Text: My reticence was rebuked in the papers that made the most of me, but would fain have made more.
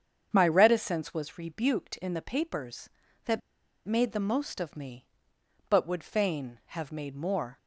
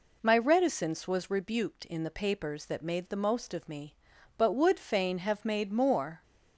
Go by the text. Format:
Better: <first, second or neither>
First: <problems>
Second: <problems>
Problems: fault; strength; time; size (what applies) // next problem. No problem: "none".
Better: second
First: starts louder than the rest; strong; until 1.3 s; 7.5 dB // pauses between "that" and "made"; noticeable; at 3.4 s; 0.46 s long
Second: none